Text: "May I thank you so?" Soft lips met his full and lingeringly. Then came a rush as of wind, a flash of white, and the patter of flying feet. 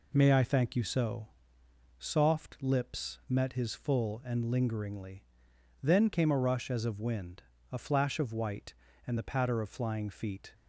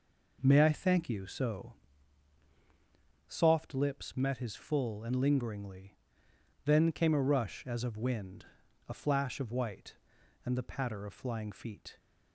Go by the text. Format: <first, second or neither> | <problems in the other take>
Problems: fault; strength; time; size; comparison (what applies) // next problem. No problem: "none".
neither | none